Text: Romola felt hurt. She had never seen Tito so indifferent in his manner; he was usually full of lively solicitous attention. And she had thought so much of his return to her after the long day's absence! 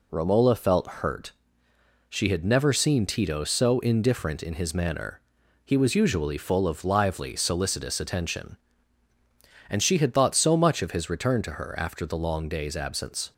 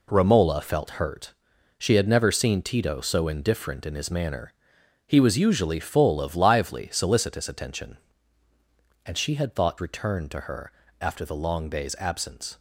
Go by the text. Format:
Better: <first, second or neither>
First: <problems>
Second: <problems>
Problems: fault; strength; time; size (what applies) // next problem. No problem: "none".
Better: first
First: none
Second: skips "so much of his"; at 9.7 s // pauses between "her" and "after"; slight; at 10.7 s; 0.30 s long